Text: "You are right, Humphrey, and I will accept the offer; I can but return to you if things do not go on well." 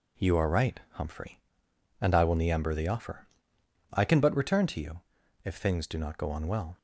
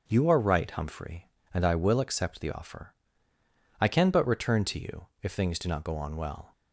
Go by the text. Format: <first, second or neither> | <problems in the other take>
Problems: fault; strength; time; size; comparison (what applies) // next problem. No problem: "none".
second | says "niember" for "accept"; at 2.3 s // pauses between "you" and "if"; at 5.0 s; 0.42 s long; slight in the second